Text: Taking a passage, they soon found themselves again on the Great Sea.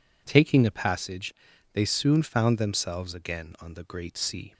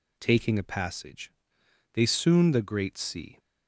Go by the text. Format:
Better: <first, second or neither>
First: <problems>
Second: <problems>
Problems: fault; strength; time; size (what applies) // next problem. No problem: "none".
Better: first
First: none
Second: skips "found themselves again on"; at 2.5 s